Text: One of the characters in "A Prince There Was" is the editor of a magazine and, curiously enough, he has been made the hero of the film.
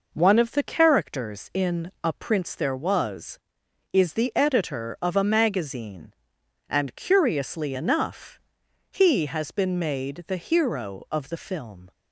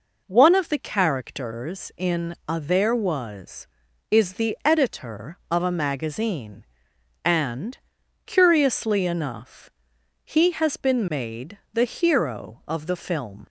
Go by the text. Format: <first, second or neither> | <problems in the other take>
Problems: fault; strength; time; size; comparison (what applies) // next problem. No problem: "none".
first | skips "Prince"; at 2.5 s